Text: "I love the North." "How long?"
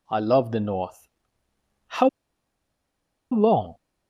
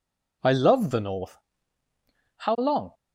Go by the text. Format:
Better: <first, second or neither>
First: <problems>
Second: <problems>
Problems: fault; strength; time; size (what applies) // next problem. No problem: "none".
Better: second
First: pauses between "How" and "long"; at 2.0 s; 1.2 s long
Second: none